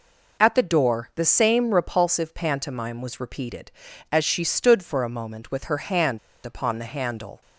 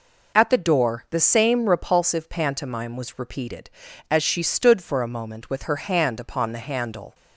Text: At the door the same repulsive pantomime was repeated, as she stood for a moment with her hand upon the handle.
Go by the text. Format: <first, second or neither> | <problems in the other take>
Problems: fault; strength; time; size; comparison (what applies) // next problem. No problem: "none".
second | pauses between "hand" and "upon"; slight; at 6.1 s; 0.25 s long